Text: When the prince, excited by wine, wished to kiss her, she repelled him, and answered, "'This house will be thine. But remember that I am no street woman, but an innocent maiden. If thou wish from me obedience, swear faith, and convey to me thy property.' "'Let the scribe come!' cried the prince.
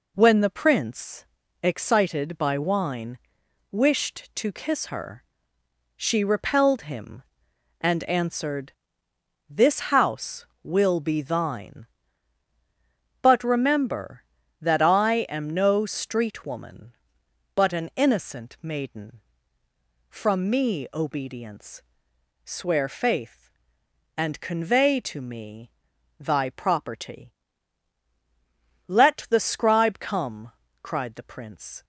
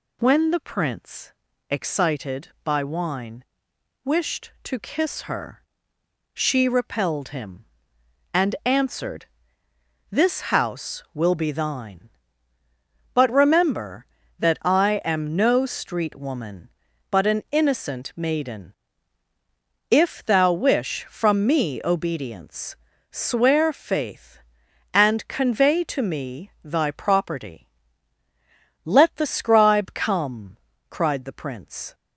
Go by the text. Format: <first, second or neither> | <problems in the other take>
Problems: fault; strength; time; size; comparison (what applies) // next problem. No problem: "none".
second | skips "If thou wish"; at 19.6 s // pauses between "me" and "thy"; noticeable; at 25.7 s; 0.48 s long